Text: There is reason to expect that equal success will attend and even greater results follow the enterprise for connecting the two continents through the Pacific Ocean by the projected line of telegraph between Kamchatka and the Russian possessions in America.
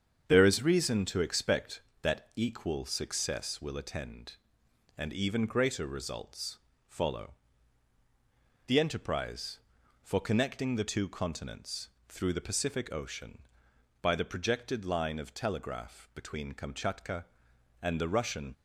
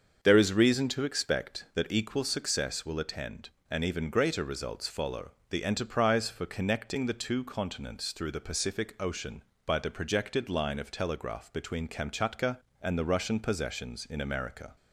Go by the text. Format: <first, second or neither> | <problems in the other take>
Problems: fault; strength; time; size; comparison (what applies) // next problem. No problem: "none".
second | starts louder than the rest; strong; until 1.3 s; 7.5 dB; also in the second // pauses between "results" and "follow"; slight; at 6.5 s; 0.30 s long // pauses between "follow" and "the"; strong; at 7.3 s; 1.3 s long; slight in the second // pauses between "continents" and "through"; slight; at 11.8 s; 0.18 s long // stops before "possessions in America"; at 18.5 s